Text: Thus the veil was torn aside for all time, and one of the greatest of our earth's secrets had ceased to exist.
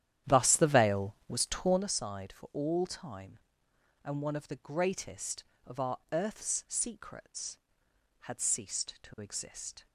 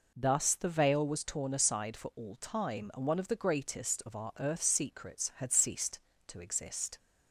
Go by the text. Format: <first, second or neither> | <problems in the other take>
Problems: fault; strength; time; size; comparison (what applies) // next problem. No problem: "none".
second | starts louder than the rest; strong; until 1.9 s; 11 dB